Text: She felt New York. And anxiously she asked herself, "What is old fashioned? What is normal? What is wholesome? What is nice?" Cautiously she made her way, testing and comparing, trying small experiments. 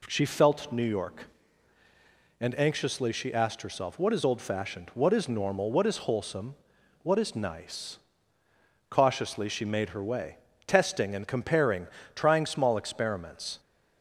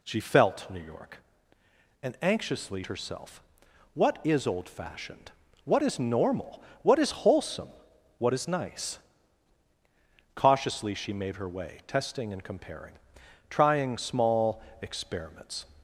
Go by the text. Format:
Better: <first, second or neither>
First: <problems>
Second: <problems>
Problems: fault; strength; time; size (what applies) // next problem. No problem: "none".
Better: first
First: none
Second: skips "she asked"; at 2.8 s // pauses between "small" and "experiments"; slight; at 14.6 s; 0.18 s long